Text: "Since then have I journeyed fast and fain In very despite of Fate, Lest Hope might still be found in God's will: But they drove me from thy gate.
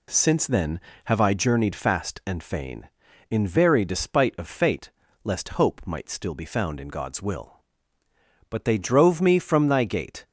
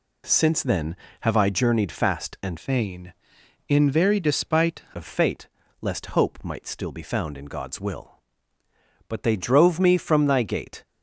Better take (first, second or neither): first